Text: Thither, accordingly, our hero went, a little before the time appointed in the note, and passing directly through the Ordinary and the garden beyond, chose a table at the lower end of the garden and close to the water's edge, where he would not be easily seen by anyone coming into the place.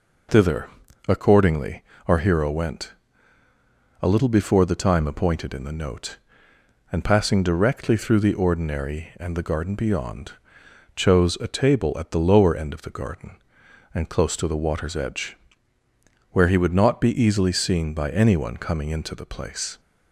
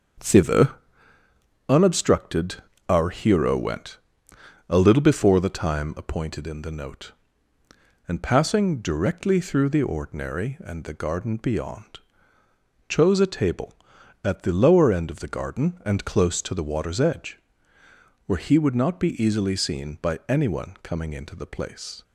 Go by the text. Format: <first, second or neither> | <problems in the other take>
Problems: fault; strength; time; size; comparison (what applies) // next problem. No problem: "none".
first | starts louder than the rest; until 2.1 s; 7 dB // says "unobstructed" for "accordingly"; at 1.6 s